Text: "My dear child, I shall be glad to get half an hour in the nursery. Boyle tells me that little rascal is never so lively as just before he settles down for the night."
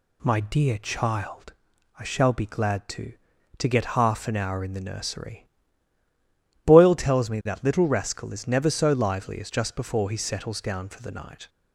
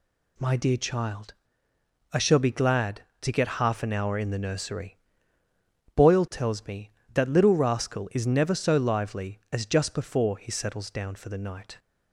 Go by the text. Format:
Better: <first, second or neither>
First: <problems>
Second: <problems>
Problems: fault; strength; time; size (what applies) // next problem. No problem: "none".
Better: second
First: says "to" twice; at 3.5 s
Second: none